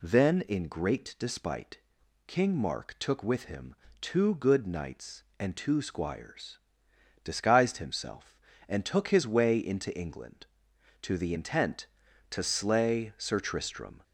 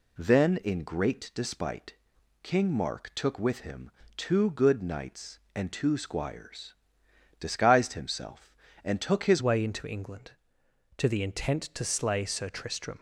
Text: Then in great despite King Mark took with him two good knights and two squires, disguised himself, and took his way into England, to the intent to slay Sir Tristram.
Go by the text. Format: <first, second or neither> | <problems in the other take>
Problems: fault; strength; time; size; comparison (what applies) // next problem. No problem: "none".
first | pauses between "despite" and "King"; noticeable; at 1.9 s; 0.48 s long; noticeable in the first // pauses between "him" and "two"; slight; at 3.8 s; 0.26 s long; slight in the first // changes voice at "way"; from 9.4 s on; 3.5 s long